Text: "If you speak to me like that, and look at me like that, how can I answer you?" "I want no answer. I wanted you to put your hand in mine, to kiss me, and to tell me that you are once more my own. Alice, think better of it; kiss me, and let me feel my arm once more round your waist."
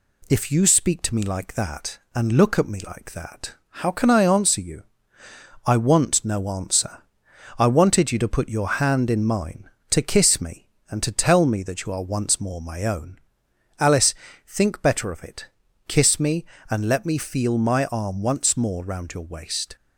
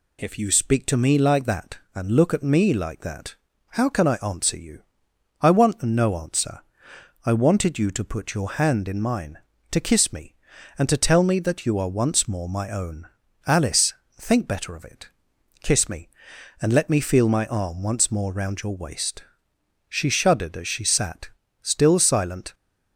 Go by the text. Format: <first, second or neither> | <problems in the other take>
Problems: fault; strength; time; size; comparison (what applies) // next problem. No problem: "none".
first | goes on to say "She shuddered as she sat still silent"; strong; from 19.8 s on; 2.6 s long